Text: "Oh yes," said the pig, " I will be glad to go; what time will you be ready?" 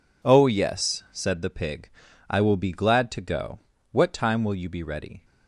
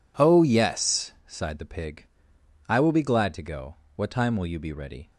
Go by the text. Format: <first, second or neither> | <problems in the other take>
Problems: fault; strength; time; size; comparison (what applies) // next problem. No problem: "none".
first | says "sighed" for "said"; at 1.2 s